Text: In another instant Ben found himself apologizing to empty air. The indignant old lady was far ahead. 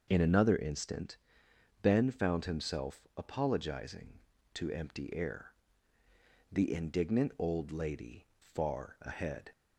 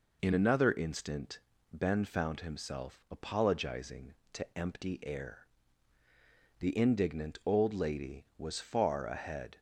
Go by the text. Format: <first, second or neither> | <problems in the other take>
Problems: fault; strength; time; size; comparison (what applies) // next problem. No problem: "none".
second | starts louder than the rest; noticeable; until 1.0 s; 6 dB // pauses between "instant" and "Ben"; noticeable; at 1.1 s; 0.66 s long; slight in the second // skips "was"; at 8.3 s